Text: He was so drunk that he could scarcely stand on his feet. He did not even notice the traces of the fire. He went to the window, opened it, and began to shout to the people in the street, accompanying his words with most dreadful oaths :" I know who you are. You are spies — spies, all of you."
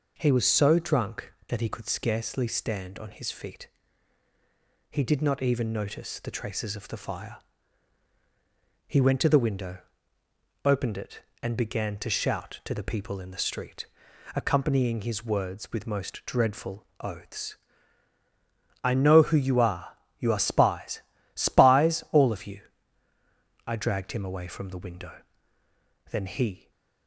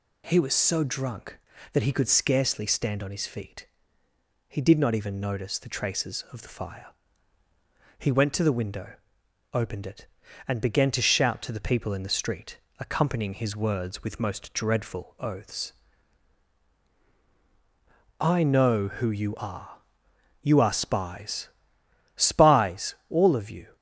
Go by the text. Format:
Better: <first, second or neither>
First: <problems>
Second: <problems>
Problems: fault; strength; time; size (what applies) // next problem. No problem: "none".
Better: second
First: goes on to say "I dragged him away from the window Then he"; strong; from 23.6 s on; 3.0 s long // stays silent after the last word; slight; from 26.5 s on; 0.5 s long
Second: none